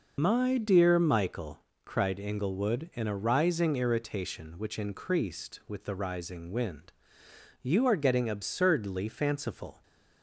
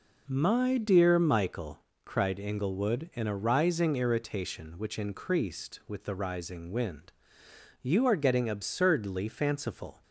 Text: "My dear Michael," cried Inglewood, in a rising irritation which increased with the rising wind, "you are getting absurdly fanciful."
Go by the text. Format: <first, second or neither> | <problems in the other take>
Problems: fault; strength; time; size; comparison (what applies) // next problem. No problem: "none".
second | loses the start of "My"; at 0.1 s; 110 ms